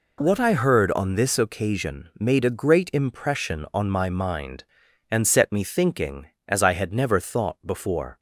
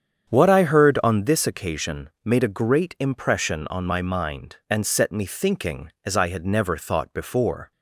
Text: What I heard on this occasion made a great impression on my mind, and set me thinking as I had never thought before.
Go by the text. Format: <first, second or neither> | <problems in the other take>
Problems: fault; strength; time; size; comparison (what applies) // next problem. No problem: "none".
first | starts louder than the rest; strong; until 1.3 s; 8.5 dB // pauses between "occasion" and "made"; slight; at 2.0 s; 0.16 s long